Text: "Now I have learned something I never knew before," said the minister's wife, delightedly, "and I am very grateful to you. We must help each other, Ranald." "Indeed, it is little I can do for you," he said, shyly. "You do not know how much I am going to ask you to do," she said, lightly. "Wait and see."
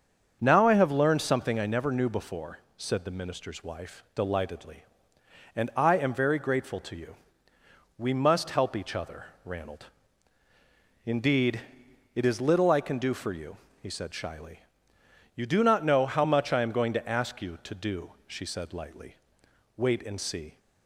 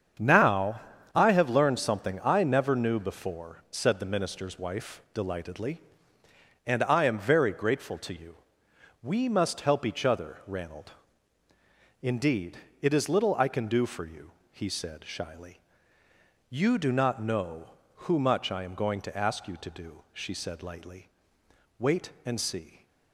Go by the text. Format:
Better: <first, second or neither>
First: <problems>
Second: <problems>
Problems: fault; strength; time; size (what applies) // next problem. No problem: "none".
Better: first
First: starts louder than the rest; until 1.4 s; 7 dB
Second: starts louder than the rest; strong; until 1.5 s; 7.5 dB // pauses between "Now" and "I"; slight; at 0.7 s; 0.35 s long // says "who" for "how"; at 18.0 s